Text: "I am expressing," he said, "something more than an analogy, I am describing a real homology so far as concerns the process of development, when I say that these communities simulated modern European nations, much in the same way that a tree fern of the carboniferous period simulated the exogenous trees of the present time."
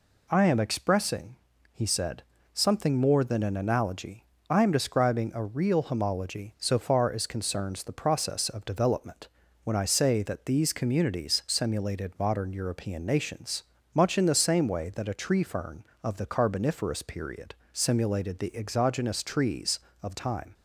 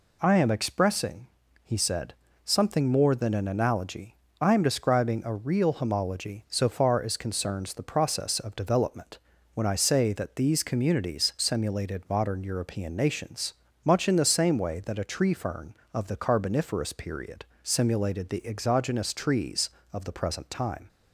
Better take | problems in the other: second | pauses between "period" and "simulated"; slight; at 17.5 s; 0.18 s long; slight in the second // skips "the present"; at 20.1 s

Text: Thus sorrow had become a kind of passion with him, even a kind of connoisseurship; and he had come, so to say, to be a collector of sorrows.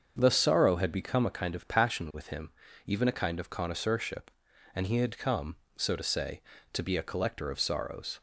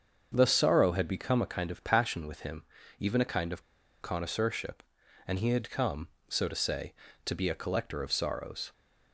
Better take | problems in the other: first | starts louder than the rest; until 1.3 s; 7 dB; also in the first // pauses between "of" and "connoisseurship"; at 3.6 s; 0.40 s long

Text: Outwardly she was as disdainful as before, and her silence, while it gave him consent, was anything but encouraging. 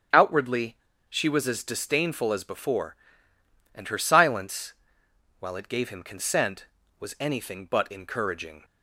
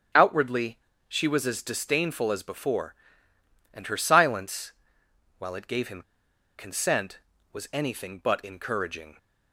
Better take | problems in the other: first | starts louder than the rest; strong; until 1.4 s; 8.5 dB; strong in the first // pauses between "Outwardly" and "she"; slight; at 0.7 s; 0.30 s long; slight in the first // pauses between "him" and "consent"; noticeable; at 6.0 s; 0.56 s long

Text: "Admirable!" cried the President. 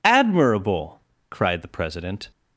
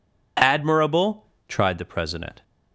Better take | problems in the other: first | says "tried" for "cried"; at 1.4 s

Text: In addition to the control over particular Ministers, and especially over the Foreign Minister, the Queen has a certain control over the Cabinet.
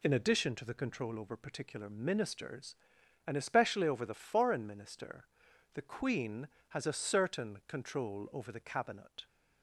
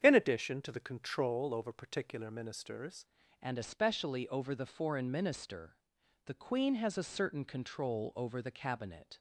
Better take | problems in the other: first | starts louder than the rest; strong; until 1.0 s; 8.5 dB // changes voice at "and"; from 3.3 s on; 5.8 s long

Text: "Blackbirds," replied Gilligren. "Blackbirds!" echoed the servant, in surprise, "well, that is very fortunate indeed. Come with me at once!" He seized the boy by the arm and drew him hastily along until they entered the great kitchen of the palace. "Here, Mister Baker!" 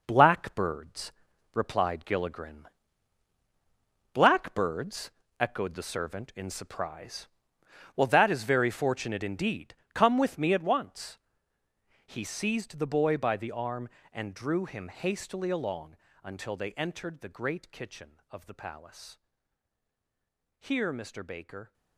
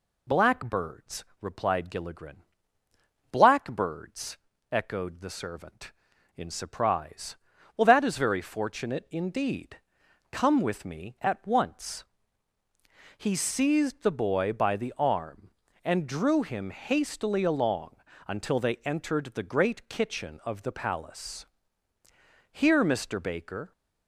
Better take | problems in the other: second | gets quieter; strong; throughout; 8 dB // pauses between "along" and "until"; slight; at 15.9 s; 0.26 s long; slight in the second

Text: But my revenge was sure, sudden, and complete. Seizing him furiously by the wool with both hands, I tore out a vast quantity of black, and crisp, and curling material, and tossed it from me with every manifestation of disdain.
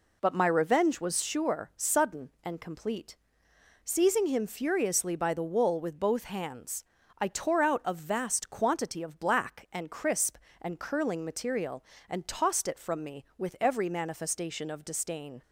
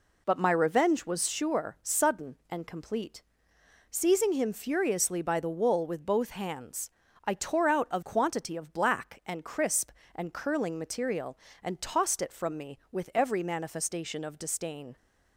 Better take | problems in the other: first | skips "vast"; at 8.0 s

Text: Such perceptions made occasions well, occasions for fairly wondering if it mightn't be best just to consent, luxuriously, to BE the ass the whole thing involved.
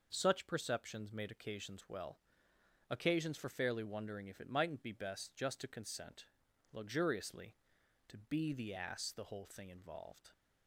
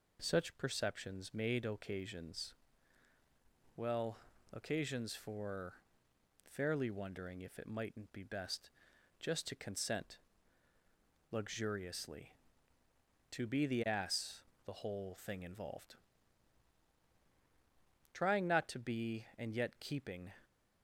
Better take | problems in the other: first | pauses between "occasions" and "well"; at 2.5 s; 1.2 s long // pauses between "for" and "fairly"; noticeable; at 5.7 s; 0.72 s long // pauses between "best" and "just"; noticeable; at 8.6 s; 0.50 s long // pauses between "ass" and "the"; slight; at 14.4 s; 0.24 s long // goes on to say "Trying not to be and yet keeping"; strong; from 18.1 s on; 2.1 s long

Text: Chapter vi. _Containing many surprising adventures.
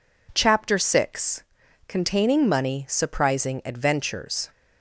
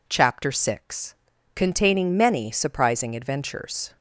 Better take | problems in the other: second | says "money" for "many"; at 2.4 s

